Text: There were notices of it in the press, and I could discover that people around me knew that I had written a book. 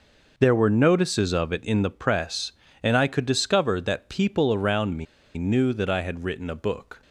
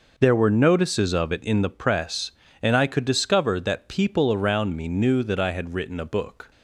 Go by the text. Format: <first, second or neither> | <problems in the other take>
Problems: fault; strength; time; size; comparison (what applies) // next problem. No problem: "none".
second | pauses between "me" and "knew"; slight; at 5.0 s; 0.32 s long